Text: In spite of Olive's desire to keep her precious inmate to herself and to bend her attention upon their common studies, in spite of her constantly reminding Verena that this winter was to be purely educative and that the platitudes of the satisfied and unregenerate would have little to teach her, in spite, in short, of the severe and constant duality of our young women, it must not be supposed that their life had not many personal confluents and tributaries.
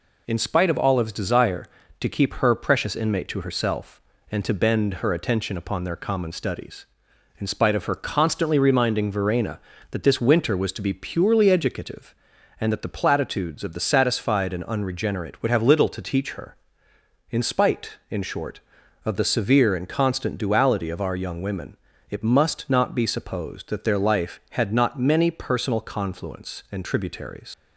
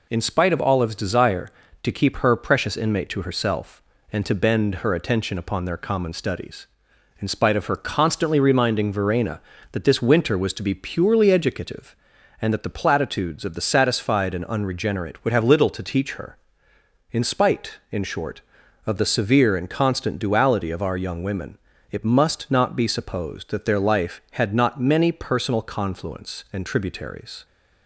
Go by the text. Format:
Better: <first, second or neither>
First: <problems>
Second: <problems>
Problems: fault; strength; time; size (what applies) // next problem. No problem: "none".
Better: second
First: leaves "tributaries" unfinished; at 27.5 s; 100 ms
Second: none